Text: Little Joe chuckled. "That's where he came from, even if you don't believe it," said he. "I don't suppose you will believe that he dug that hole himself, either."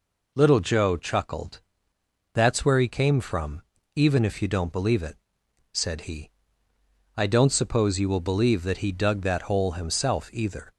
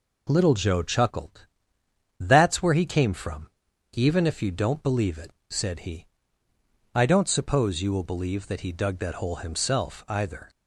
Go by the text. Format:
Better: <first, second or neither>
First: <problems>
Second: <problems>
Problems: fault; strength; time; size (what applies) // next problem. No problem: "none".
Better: neither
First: none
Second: none